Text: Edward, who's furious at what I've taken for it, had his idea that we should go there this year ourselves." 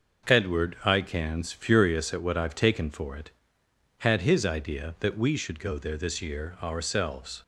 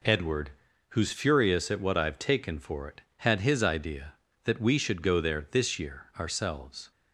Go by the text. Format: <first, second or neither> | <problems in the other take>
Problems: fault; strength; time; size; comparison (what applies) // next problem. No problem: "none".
second | says "icans" for "who's"; at 0.8 s